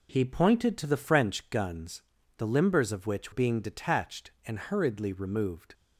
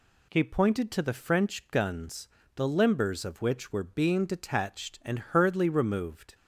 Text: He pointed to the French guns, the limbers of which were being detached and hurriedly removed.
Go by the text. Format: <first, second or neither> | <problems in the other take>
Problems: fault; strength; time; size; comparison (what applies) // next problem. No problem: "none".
second | skips "were"; at 3.3 s